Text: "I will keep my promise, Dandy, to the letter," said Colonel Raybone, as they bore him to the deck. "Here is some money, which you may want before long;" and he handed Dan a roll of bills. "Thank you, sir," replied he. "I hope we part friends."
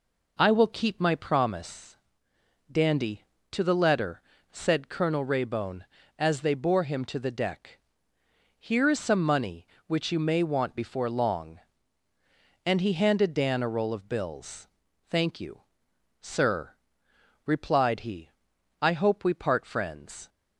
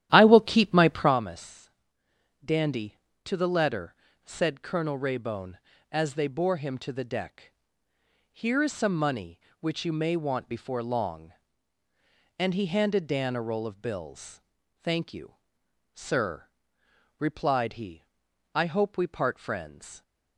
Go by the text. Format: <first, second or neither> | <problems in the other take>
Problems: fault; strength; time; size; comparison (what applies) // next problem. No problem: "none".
first | starts louder than the rest; strong; until 1.2 s; 12.5 dB